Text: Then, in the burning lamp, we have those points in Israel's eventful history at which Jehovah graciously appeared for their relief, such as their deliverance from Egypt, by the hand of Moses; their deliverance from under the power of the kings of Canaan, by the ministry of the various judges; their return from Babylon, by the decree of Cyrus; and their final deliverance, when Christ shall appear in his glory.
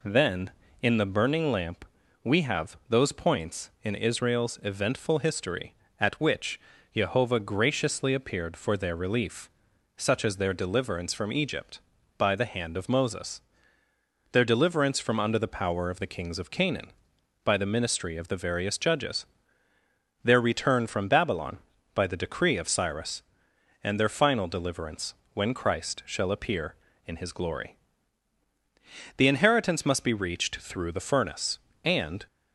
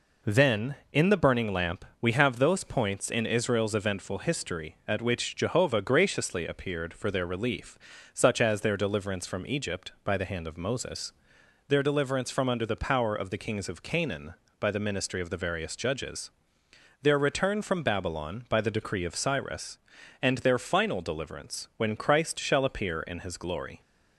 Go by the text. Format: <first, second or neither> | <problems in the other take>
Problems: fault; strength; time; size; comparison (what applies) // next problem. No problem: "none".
second | pauses between "which" and "Jehovah"; slight; at 6.5 s; 0.36 s long // goes on to say "The inheritance must be reached through the furnace and"; strong; from 29.1 s on; 3.1 s long